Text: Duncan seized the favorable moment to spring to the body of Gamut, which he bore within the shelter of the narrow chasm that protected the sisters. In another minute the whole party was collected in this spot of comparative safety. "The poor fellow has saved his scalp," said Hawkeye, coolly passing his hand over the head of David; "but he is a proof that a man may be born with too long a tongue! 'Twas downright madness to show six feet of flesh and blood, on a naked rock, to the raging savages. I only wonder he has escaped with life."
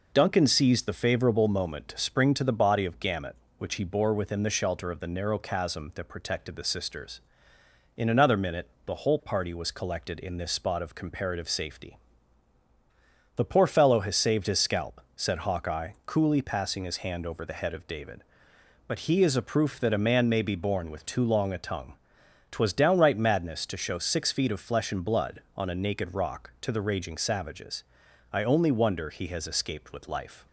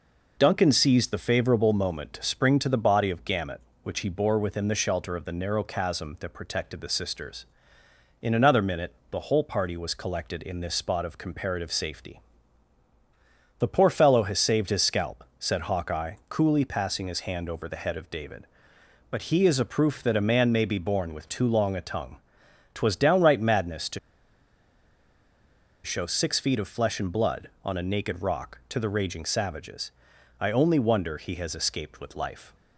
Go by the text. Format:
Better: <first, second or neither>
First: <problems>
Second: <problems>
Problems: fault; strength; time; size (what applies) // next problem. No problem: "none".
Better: first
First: pauses between "minute" and "the"; slight; at 8.6 s; 0.18 s long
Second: pauses between "minute" and "the"; slight; at 8.9 s; 0.18 s long // pauses between "to" and "show"; strong; at 23.9 s; 1.8 s long